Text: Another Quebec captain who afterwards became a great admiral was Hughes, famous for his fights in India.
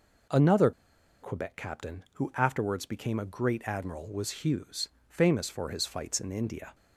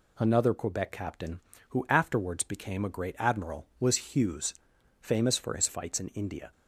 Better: second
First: pauses between "Another" and "Quebec"; noticeable; at 0.7 s; 0.50 s long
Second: none

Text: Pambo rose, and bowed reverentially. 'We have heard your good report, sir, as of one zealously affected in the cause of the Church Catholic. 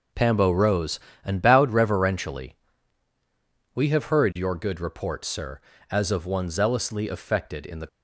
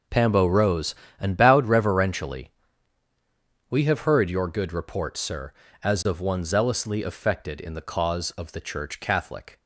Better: second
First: stops before "cause of the Church Catholic"; at 7.8 s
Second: none

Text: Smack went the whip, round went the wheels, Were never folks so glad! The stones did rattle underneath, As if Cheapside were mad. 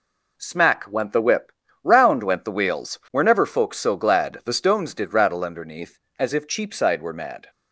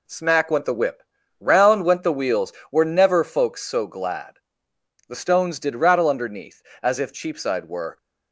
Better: first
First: none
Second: stops before "mad"; at 7.9 s

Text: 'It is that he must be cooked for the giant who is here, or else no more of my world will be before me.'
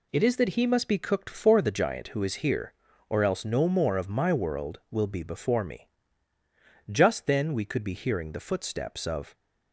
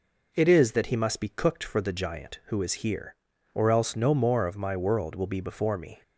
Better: second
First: goes on to say "Just then we could be hearing the footsteps of"; strong; from 6.9 s on; 2.4 s long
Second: none

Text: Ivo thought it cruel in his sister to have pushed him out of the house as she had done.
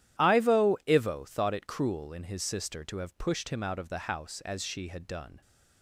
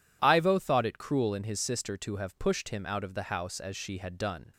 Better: second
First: says "Ivo" twice; at 0.8 s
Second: none

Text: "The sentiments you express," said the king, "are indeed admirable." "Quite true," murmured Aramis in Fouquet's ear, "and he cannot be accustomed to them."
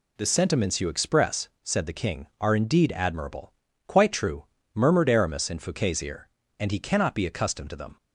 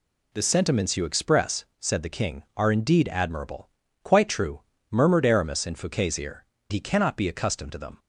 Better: first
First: none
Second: skips "and"; at 6.5 s

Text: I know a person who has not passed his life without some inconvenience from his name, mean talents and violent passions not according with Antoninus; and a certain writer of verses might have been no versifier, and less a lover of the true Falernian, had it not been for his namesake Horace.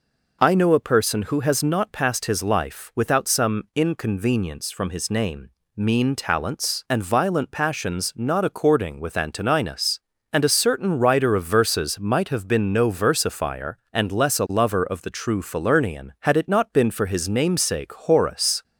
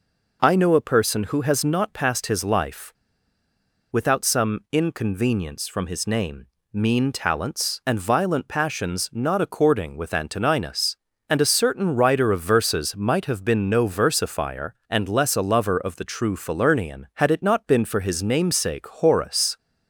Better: first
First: none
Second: pauses between "life" and "without"; noticeable; at 2.9 s; 0.97 s long

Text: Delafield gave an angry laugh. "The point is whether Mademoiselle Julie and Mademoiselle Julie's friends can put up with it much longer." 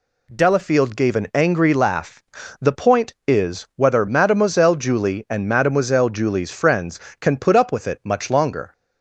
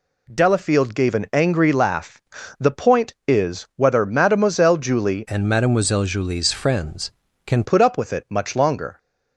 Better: first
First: none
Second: changes voice from "and" to "can"; from 5.2 to 7.6 s; 2.4 s long

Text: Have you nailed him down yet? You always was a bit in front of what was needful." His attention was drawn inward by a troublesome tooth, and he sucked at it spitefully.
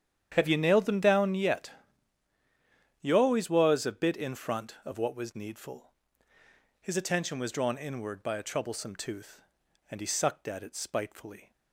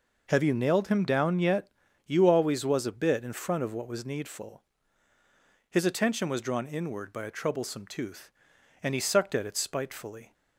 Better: second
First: starts louder than the rest; strong; until 1.3 s; 9 dB // says "them" for "him"; at 0.8 s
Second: none

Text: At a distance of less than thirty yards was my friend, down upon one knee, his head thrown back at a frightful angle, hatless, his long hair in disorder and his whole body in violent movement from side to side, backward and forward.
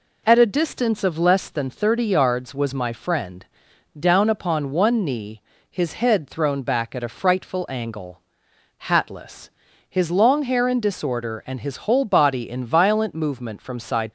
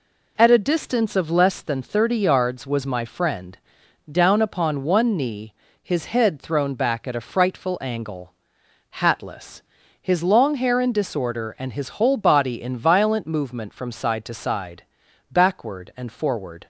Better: second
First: stops before "to side backward and forward"; at 14.0 s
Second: none

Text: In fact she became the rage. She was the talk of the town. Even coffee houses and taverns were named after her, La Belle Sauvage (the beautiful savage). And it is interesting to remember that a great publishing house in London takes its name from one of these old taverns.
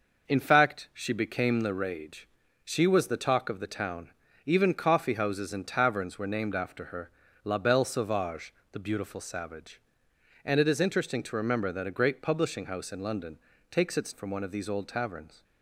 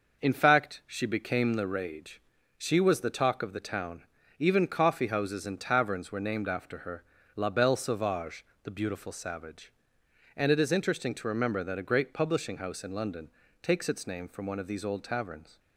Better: second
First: pauses between "London" and "takes"; slight; at 13.3 s; 0.32 s long // skips "name"; at 14.1 s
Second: pauses between "London" and "takes"; slight; at 13.2 s; 0.32 s long

